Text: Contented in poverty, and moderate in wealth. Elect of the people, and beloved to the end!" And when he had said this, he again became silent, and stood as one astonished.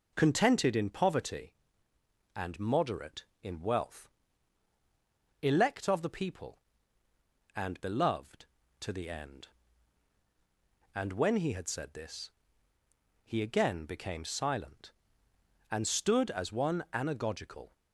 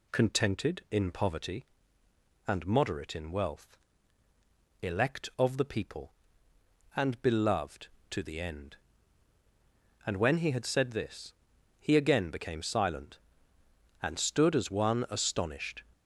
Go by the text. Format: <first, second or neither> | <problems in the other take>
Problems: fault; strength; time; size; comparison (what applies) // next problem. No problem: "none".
second | says "anagogical" for "astonished"; at 16.9 s